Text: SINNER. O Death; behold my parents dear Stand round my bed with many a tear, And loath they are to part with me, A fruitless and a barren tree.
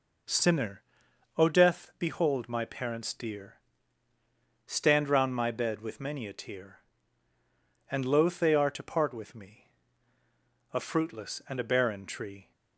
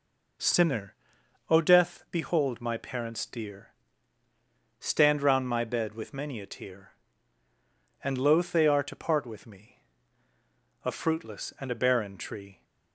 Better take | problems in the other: neither | pauses between "dear" and "Stand"; the same in both

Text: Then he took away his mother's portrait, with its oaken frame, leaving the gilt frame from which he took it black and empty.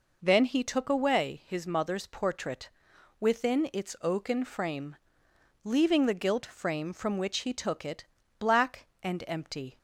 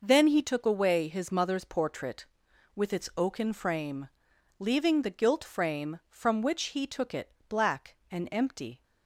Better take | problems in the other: second | says "within" for "with"; at 3.1 s // pauses between "it" and "black"; slight; at 8.0 s; 0.32 s long; slight in the second

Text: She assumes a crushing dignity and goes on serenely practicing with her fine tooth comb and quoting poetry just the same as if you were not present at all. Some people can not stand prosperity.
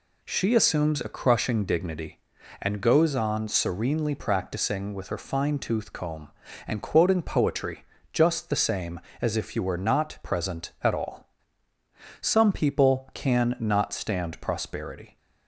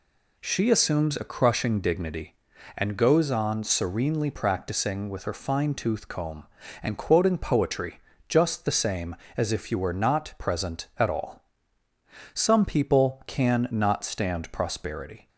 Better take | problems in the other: neither | pauses between "poetry" and "just"; slight; the same in both

